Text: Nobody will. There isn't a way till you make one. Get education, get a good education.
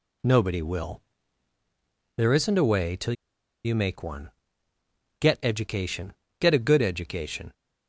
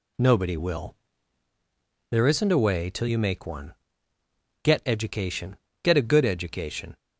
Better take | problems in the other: second | pauses between "till" and "you"; noticeable; at 3.1 s; 0.51 s long

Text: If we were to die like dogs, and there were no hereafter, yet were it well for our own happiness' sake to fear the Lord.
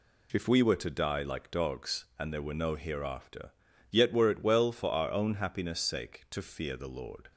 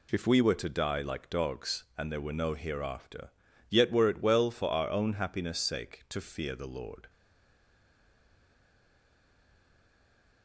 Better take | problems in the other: first | stays silent after the last word; strong; from 7.0 s on; 3.4 s long

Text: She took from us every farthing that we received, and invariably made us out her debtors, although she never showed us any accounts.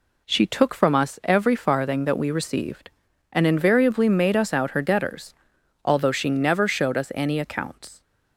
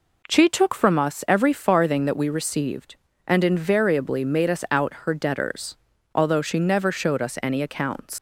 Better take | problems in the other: first | leaves "accounts" unfinished; at 8.1 s; 80 ms

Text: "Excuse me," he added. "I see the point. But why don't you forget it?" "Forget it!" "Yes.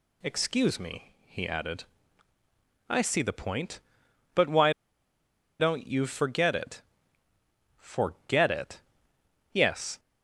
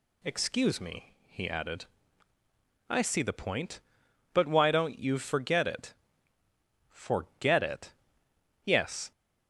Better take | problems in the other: second | pauses between "why" and "don't"; noticeable; at 4.7 s; 0.89 s long

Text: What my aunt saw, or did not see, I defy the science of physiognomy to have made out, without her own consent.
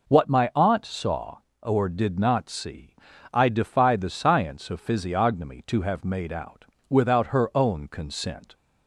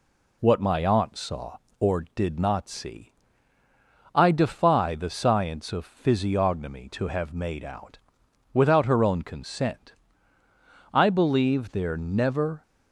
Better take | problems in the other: first | goes on to say "I believe there never"; strong; from 10.9 s on; 1.7 s long

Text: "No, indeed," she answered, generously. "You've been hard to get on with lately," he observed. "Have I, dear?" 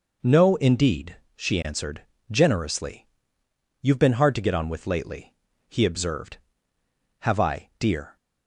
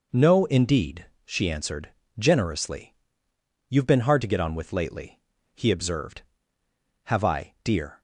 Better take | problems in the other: neither | none

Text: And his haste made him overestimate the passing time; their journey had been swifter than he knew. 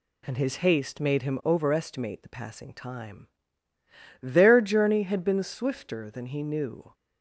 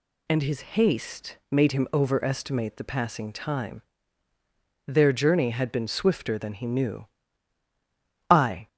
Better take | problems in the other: first | goes on to say "I"; slight; from 8.2 s on; 0.38 s long

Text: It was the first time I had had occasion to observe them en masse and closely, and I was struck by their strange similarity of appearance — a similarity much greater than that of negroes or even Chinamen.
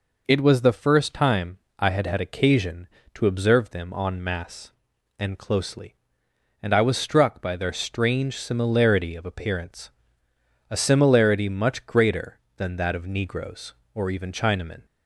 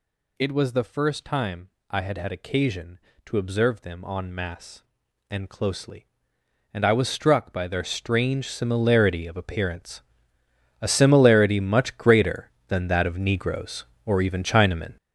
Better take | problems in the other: first | gets louder; strong; throughout; 8 dB // pauses between "time" and "I"; slight; at 1.7 s; 0.18 s long; slight in the first

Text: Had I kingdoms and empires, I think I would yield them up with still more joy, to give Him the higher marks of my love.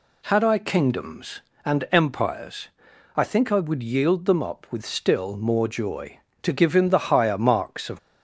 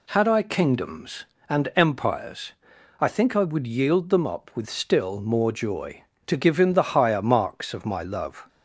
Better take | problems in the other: second | stops before "my love"; at 7.9 s

